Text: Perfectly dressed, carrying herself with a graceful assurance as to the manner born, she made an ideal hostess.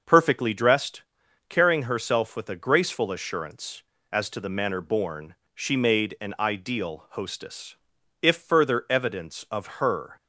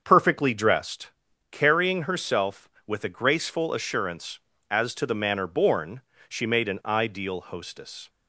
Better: second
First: starts louder than the rest; until 1.5 s; 6 dB // goes on to say "If further evidence of her"; strong; from 8.2 s on; 1.9 s long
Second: starts louder than the rest; until 1.0 s; 7 dB

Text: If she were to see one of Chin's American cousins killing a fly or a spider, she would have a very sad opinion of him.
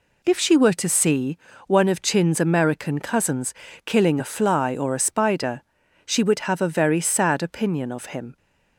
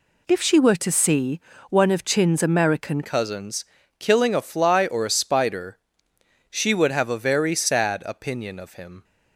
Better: first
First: pauses between "see" and "one"; slight; at 1.3 s; 0.30 s long // pauses between "cousins" and "killing"; slight; at 3.5 s; 0.34 s long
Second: pauses between "see" and "one"; slight; at 1.3 s; 0.30 s long // changes voice at "cousins"; from 3.0 s on; 6.0 s long // pauses between "cousins" and "killing"; slight; at 3.6 s; 0.36 s long

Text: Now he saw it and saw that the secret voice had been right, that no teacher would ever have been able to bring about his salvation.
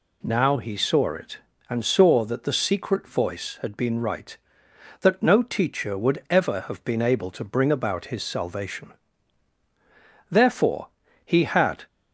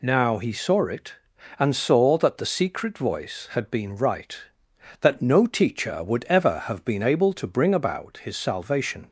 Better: second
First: goes on to say "Therefore he had"; from 10.2 s on; 1.5 s long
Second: none

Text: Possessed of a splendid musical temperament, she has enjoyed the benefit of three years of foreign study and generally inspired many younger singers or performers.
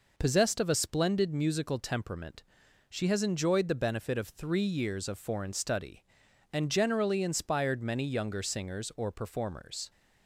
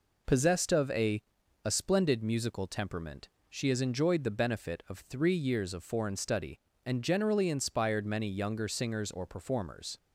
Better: first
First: none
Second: says "a" twice; at 1.6 s

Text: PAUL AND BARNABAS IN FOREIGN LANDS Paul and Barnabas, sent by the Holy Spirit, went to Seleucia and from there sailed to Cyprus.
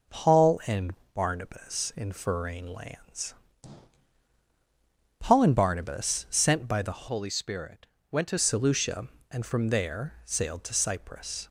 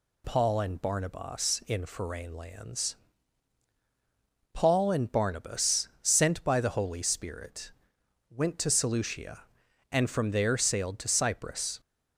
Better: second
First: pauses between "AND" and "BARNABAS"; slight; at 0.9 s; 0.20 s long // pauses between "LANDS" and "Paul"; strong; at 3.3 s; 1.8 s long // changes voice from "Holy" to "to"; from 7.0 to 8.3 s; 1.3 s long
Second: pauses between "LANDS" and "Paul"; strong; at 2.9 s; 1.5 s long

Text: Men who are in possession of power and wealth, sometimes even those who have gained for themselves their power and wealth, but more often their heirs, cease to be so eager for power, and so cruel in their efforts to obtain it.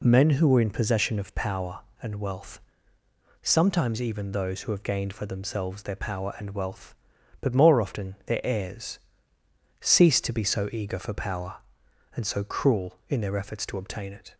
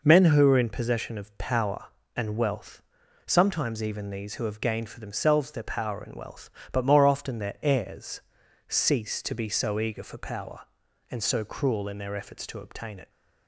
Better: first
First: none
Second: says "these" for "those"; at 4.1 s

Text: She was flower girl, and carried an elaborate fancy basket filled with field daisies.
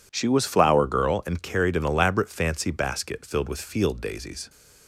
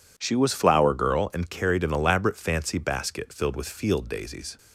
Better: neither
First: none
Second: none

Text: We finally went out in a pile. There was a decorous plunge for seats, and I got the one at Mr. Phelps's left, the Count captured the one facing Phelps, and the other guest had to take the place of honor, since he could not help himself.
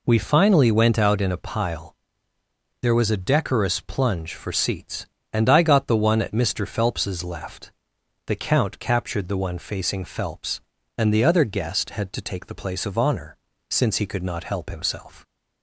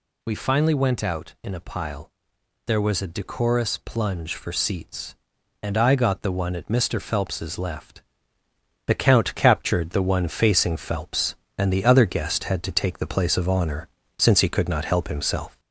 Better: first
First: none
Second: gets louder; slight; throughout; 2.5 dB

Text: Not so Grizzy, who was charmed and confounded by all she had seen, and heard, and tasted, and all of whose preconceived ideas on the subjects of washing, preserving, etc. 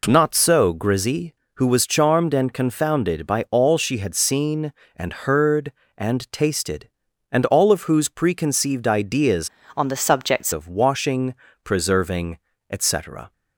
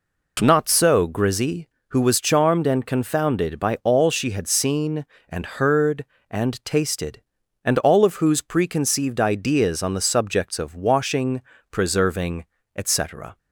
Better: second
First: changes voice from "on" to "subjects"; from 9.7 to 10.5 s; 0.8 s long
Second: none

